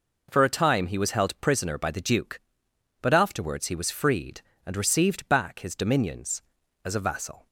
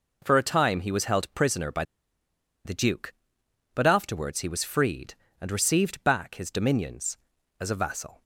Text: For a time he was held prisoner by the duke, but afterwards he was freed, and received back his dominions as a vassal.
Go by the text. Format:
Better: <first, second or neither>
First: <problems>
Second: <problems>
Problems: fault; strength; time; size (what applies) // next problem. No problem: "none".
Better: first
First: none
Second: pauses between "by" and "the"; noticeable; at 1.8 s; 0.82 s long